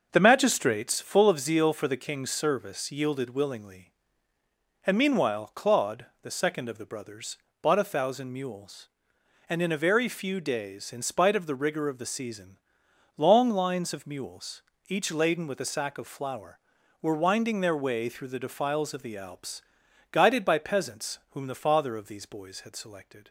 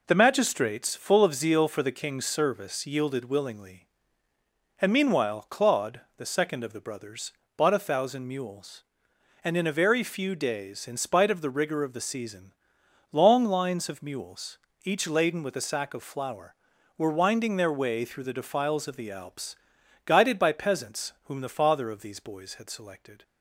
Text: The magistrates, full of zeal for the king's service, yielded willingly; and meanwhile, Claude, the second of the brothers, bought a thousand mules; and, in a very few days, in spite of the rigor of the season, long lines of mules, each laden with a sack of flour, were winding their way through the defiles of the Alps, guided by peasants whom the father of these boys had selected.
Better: second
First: starts louder than the rest; until 1.3 s; 6 dB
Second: none

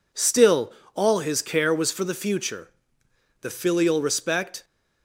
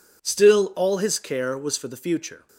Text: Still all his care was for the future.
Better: second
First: pauses between "Still" and "all"; slight; at 0.7 s; 0.22 s long // goes on to say "The filial respect"; noticeable; from 3.3 s on; 1.2 s long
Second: none

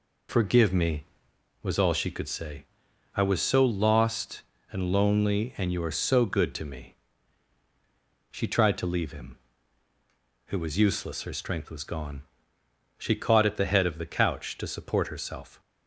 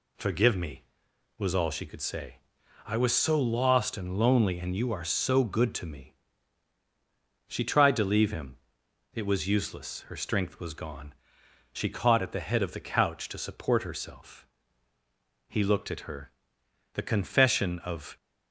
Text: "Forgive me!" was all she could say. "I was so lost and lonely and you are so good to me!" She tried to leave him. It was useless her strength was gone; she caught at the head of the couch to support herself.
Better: first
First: none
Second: goes on to say "He looked at her The confession of"; strong; from 15.4 s on; 2.6 s long

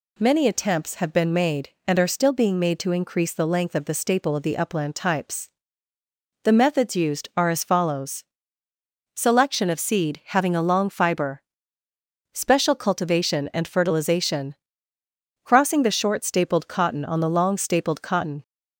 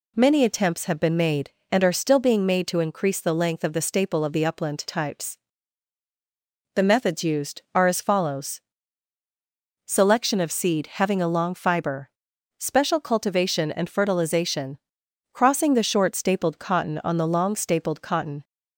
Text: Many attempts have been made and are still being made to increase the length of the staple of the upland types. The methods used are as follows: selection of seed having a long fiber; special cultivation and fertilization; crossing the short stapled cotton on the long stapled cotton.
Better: neither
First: none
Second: none

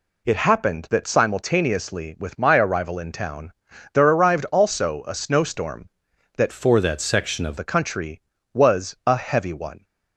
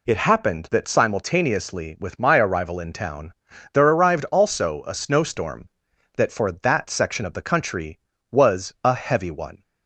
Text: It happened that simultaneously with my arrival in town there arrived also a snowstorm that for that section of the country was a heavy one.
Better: second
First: pauses between "town" and "there"; at 3.5 s; 0.42 s long // changes voice from "for" to "of"; from 6.5 to 7.5 s; 1.0 s long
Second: pauses between "town" and "there"; at 3.3 s; 0.41 s long

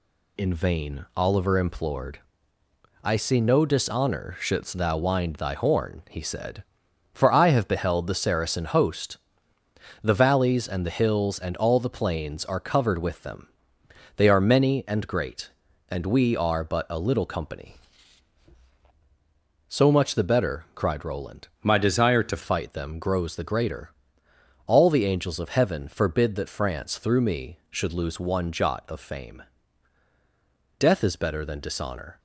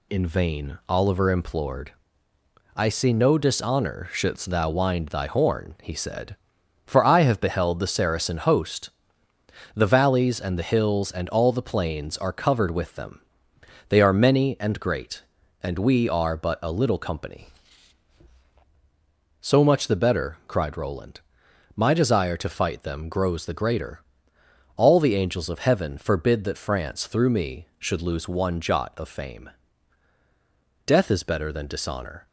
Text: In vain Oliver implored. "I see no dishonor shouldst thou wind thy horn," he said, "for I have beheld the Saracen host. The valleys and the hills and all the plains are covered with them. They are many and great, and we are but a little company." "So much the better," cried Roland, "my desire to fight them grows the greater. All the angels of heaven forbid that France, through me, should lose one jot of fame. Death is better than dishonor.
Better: second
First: changes voice from "my" to "to"; from 21.6 to 22.4 s; 0.8 s long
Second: none

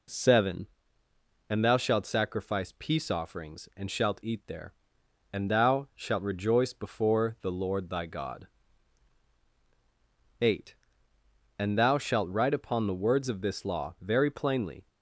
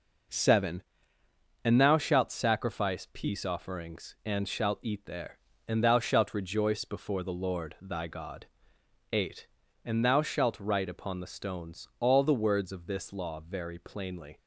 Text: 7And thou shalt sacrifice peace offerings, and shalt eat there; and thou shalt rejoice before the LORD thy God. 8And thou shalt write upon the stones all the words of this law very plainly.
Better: second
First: skips "stones all the"; at 12.9 s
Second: none

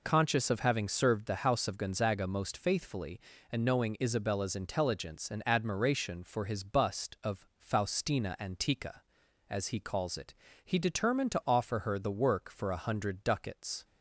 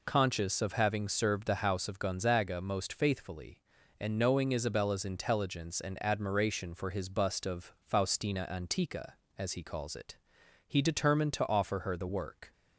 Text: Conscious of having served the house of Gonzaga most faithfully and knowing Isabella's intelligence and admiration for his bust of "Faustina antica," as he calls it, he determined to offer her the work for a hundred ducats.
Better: first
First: none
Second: stops before "for a hundred ducats"; at 12.5 s

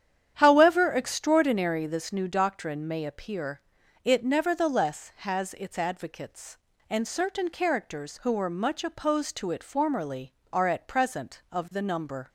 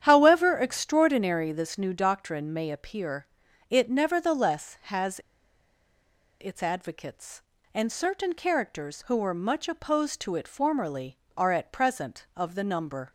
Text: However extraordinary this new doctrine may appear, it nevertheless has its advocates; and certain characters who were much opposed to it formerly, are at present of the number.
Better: first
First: starts louder than the rest; strong; until 1.3 s; 9.5 dB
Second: starts louder than the rest; strong; until 1.0 s; 9.5 dB // pauses between "has" and "its"; at 5.1 s; 1.2 s long

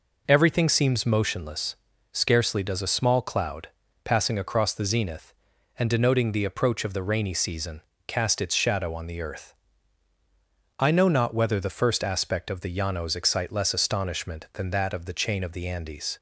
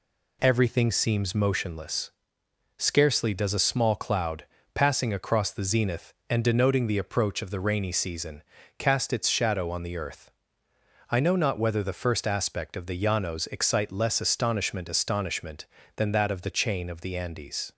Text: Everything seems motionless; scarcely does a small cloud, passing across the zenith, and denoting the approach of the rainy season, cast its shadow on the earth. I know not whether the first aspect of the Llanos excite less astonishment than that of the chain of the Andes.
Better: first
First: none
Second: says "astonishment" twice; at 14.8 s

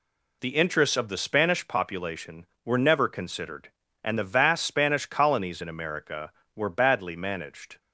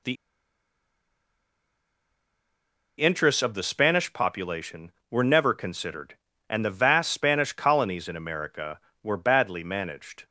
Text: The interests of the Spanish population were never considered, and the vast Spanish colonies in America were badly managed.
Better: first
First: none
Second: pauses between "The" and "interests"; strong; at 0.1 s; 2.8 s long

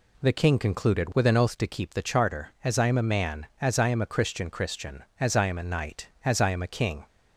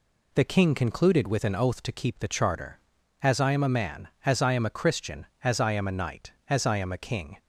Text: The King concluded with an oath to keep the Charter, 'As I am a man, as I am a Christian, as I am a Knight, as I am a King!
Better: second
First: says "Christian" twice; at 4.4 s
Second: none

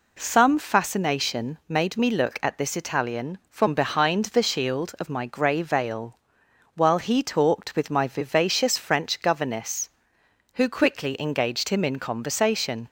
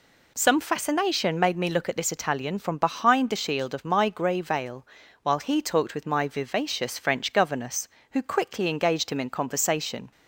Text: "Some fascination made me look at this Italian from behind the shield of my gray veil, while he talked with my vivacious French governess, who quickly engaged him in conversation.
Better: neither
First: none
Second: none

